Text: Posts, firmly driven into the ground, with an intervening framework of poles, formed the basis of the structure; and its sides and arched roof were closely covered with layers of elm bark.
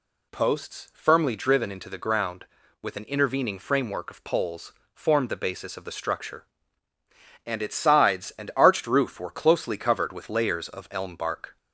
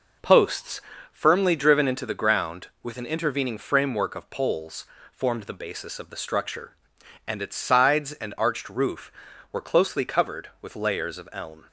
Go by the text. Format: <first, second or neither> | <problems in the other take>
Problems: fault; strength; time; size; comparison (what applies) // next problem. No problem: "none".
first | stops before "bark"; at 11.6 s